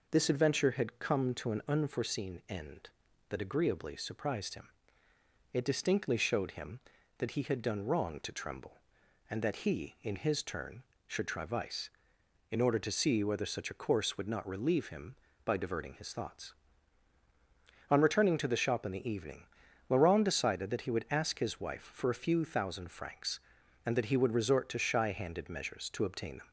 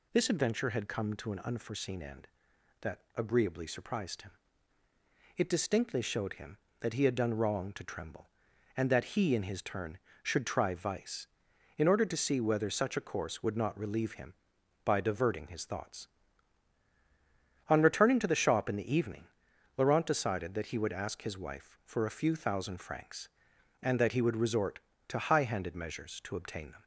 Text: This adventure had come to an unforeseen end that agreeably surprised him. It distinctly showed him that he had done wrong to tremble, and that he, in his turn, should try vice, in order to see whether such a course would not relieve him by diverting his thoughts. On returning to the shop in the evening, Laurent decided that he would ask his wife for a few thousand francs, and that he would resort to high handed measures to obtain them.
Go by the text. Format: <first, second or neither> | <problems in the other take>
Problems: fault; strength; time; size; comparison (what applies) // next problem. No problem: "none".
second | says "shy" for "high"; at 24.7 s